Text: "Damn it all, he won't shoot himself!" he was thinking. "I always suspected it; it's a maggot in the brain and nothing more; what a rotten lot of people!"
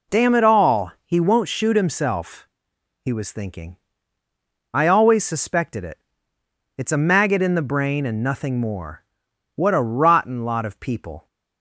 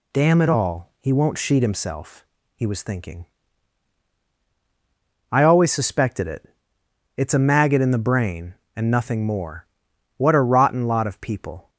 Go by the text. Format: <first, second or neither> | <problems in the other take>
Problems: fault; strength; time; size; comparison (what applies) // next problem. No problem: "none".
first | says "sheet" for "shoot"; at 1.3 s